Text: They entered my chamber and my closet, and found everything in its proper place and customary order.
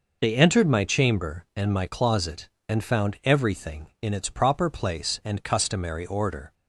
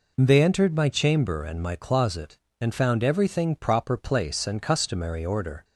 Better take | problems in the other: first | skips "in its"; at 3.5 s

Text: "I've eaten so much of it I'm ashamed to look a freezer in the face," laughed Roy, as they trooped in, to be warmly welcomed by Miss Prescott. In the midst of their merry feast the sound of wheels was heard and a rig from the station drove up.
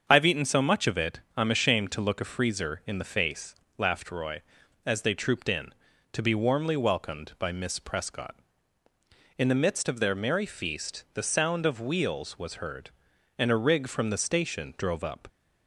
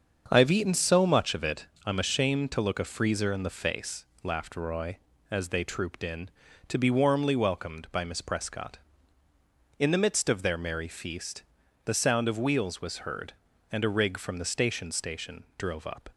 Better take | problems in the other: first | starts louder than the rest; until 1.2 s; 7 dB; also in the first // pauses between "it" and "I'm"; slight; at 1.6 s; 0.18 s long; slight in the first // pauses between "feast" and "the"; at 11.4 s; 0.42 s long // says "station" twice; at 14.9 s

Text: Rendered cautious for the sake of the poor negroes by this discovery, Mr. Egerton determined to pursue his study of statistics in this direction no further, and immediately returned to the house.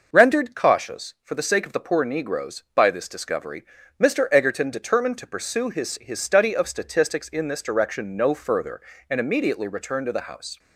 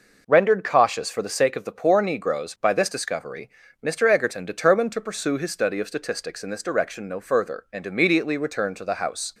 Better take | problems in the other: second | says "his" twice; at 6.0 s

